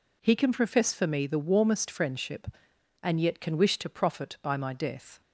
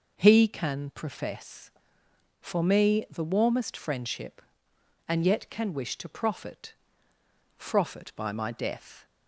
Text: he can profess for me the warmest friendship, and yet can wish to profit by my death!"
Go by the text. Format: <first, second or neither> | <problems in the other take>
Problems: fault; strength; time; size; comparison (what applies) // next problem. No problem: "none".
first | says "profit" twice; at 7.5 s